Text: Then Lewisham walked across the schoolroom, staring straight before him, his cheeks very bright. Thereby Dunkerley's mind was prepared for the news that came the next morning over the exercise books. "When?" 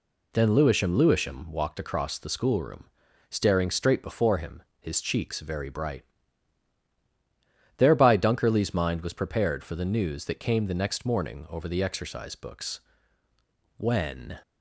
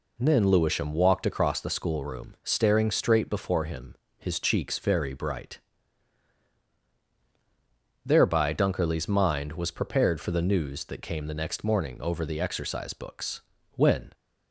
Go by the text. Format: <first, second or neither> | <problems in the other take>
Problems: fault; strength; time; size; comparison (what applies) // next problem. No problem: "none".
second | says "Lewisham" twice; at 0.9 s